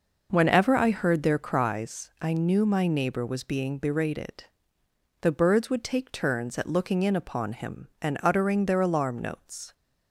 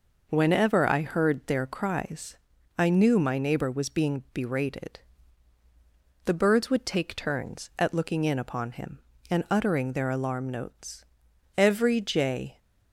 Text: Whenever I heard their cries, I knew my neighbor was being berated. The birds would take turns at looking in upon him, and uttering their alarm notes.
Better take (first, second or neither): first